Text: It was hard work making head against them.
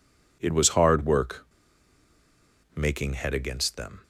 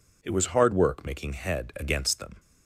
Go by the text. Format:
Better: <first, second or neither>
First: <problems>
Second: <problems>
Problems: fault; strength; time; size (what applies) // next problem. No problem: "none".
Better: second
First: pauses between "work" and "making"; strong; at 1.4 s; 1.3 s long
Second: none